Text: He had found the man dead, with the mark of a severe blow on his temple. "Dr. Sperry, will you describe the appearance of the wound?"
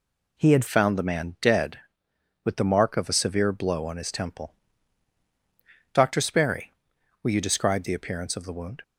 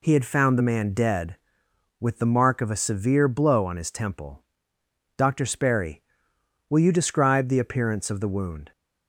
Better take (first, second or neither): second